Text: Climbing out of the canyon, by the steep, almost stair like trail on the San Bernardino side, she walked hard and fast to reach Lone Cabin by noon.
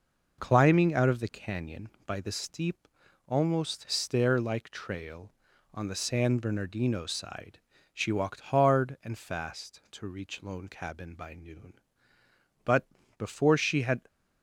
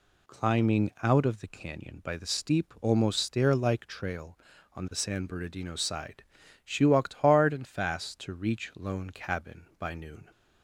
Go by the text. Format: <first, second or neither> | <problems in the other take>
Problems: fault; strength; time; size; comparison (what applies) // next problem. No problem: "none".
second | goes on to say "But before she had"; from 12.6 s on; 1.3 s long